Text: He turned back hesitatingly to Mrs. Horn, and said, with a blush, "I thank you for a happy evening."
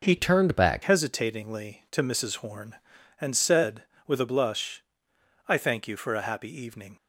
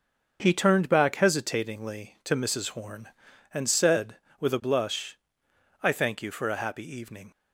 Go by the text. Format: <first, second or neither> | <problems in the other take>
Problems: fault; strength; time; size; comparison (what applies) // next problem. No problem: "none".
second | changes voice from "turned" to "back"; from 0.1 to 0.8 s; 0.7 s long